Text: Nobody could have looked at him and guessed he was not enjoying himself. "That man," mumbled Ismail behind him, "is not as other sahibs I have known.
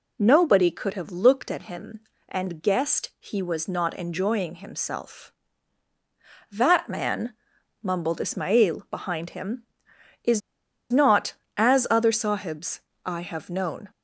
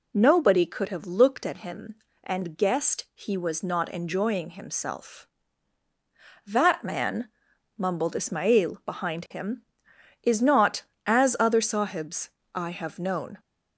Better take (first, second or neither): second